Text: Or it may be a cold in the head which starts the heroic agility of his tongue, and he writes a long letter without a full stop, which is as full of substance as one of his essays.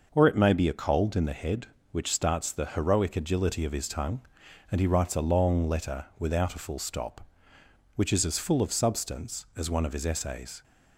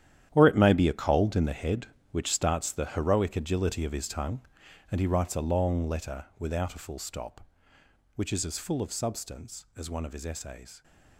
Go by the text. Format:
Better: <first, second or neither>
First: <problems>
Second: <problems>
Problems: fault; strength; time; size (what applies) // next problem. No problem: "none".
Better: first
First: none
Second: gets quieter; strong; throughout; 12.5 dB